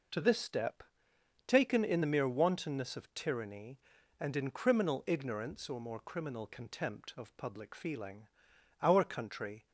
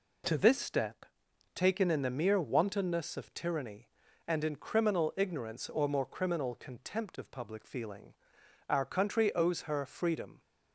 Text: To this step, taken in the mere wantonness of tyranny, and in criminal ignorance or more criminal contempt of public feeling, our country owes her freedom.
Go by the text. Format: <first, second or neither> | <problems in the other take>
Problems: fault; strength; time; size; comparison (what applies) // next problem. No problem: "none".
second | stops before "owes her freedom"; at 9.6 s